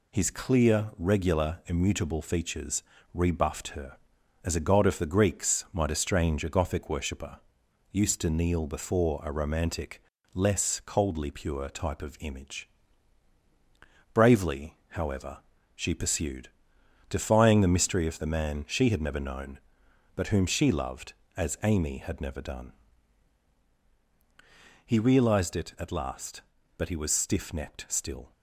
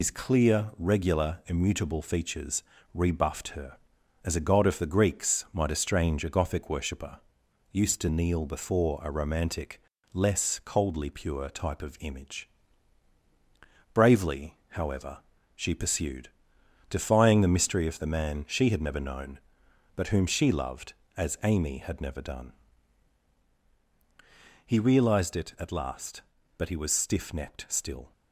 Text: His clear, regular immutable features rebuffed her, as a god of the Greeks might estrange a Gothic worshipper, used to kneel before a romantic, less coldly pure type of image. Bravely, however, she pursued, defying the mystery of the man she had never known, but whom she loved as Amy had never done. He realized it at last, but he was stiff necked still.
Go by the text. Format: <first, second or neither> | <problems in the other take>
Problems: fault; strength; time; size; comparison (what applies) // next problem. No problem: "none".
first | loses the start of "His"; at 0.0 s; 100 ms // pauses between "features" and "rebuffed"; slight; at 2.6 s; 0.30 s long; slight in the first